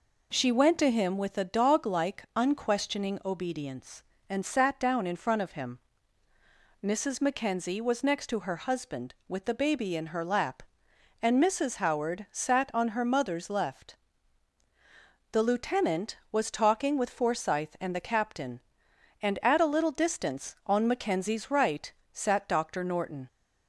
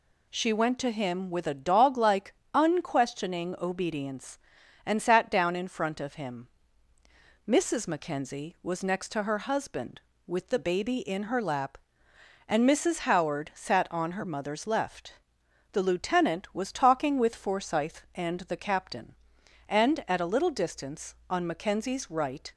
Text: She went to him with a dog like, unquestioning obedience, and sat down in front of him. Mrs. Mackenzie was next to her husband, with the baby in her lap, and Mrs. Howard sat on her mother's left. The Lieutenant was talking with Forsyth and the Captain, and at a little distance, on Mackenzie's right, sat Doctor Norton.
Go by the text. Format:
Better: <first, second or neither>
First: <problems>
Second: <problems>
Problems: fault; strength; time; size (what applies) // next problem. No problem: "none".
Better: first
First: none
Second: stops before "sat Doctor Norton"; at 22.5 s